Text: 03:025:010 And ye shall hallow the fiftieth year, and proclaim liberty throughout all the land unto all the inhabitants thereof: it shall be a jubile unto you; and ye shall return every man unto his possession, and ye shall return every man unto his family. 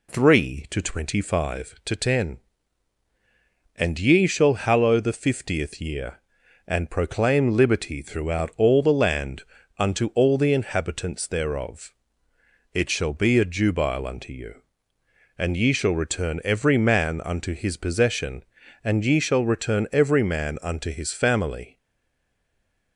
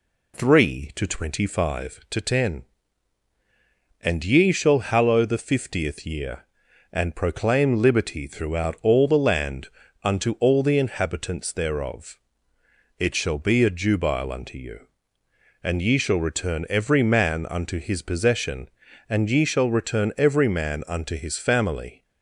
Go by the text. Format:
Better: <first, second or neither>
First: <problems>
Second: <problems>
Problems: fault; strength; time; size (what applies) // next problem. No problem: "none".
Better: second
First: pauses between "land" and "unto"; slight; at 9.4 s; 0.34 s long // stays silent after the last word; noticeable; from 21.7 s on; 1.2 s long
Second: pauses between "land" and "unto"; slight; at 9.6 s; 0.34 s long